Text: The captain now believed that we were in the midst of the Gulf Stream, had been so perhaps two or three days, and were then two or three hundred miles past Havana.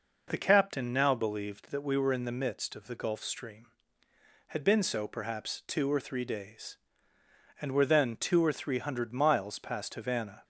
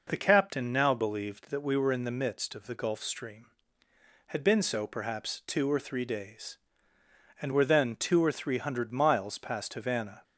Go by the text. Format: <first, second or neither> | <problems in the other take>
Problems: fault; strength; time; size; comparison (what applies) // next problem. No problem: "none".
neither | none